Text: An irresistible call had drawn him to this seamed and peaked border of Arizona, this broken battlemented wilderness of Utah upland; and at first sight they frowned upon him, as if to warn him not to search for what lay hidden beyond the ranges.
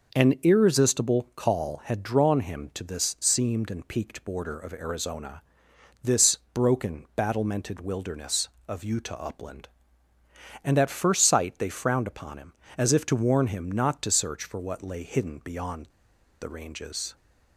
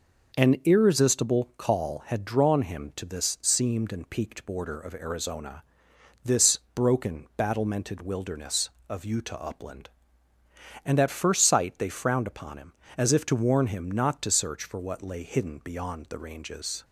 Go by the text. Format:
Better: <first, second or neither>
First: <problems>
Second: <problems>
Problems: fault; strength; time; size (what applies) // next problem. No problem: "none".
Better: second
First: pauses between "this" and "broken"; slight; at 6.3 s; 0.16 s long // pauses between "beyond" and "the"; noticeable; at 15.8 s; 0.54 s long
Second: pauses between "this" and "broken"; slight; at 6.5 s; 0.16 s long